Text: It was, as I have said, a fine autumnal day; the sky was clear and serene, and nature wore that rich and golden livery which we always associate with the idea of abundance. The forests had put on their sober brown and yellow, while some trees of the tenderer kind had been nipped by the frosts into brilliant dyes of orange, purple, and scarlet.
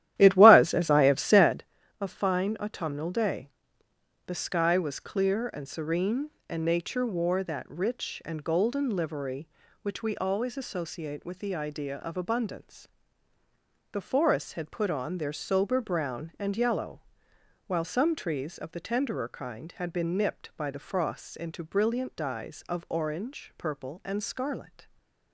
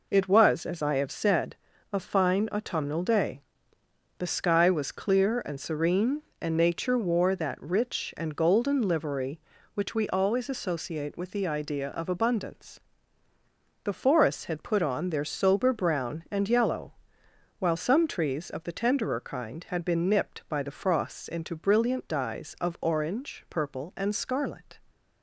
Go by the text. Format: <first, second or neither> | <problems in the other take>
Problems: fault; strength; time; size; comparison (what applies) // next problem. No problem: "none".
second | starts louder than the rest; strong; until 1.7 s; 13 dB // stays silent after the last word; slight; from 24.8 s on; 0.5 s long